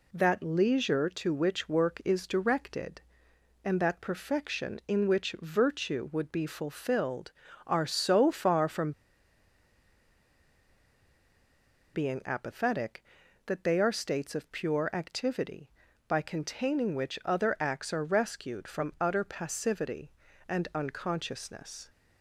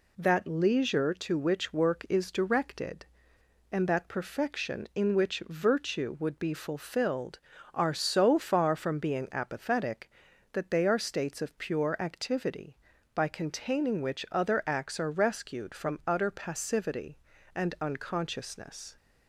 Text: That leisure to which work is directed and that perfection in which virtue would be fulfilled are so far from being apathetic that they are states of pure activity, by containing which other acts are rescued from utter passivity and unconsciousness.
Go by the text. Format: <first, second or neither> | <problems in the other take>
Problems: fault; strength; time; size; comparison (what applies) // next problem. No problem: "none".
second | pauses between "from" and "being"; strong; at 8.9 s; 3.0 s long